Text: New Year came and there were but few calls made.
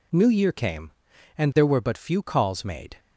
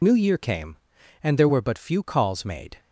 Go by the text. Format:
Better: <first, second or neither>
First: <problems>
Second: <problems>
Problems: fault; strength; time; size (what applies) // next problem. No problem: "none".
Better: first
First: none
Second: loses the start of "New"; at 0.0 s; 45 ms